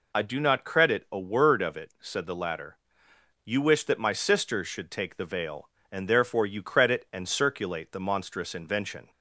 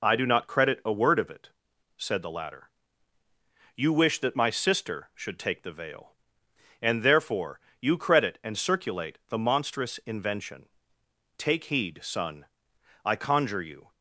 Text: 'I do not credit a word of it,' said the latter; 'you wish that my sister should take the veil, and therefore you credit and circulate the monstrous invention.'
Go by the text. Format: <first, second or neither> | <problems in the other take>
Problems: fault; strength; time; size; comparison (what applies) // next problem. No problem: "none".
first | pauses between "therefore" and "you"; slight; at 7.5 s; 0.22 s long // goes on to say "Take heed son I conjure you"; strong; from 11.3 s on; 2.5 s long